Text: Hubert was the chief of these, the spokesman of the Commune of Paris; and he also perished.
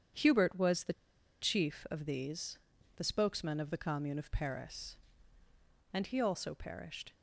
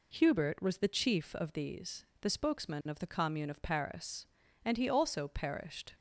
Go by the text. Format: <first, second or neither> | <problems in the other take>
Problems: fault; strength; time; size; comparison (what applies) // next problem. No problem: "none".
second | starts louder than the rest; strong; until 1.6 s; 8.5 dB // pauses between "the" and "chief"; noticeable; at 0.9 s; 0.48 s long